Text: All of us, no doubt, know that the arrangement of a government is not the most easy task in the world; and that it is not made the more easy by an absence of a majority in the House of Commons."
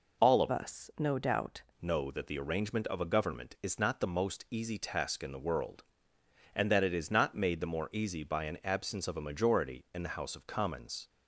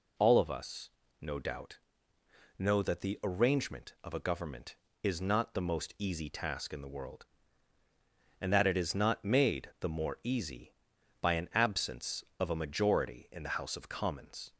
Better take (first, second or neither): second